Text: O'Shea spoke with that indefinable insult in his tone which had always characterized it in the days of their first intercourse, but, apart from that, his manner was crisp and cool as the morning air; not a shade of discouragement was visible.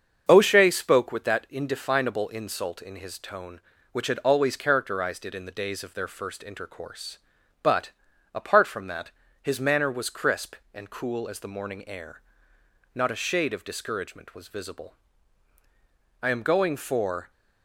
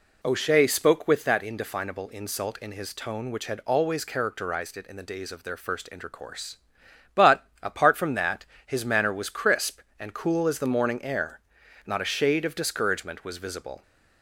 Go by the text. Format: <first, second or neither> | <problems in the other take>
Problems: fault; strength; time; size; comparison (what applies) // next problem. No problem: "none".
second | starts louder than the rest; until 1.2 s; 7 dB // goes on to say "I am going for"; noticeable; from 16.2 s on; 1.1 s long